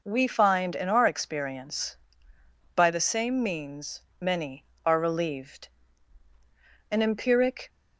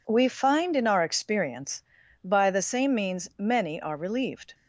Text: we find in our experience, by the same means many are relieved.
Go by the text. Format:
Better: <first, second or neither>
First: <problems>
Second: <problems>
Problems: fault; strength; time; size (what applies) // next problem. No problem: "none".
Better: second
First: pauses between "means" and "many"; slight; at 4.0 s; 0.20 s long // goes on to say "An empiric"; noticeable; from 6.8 s on; 0.80 s long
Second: none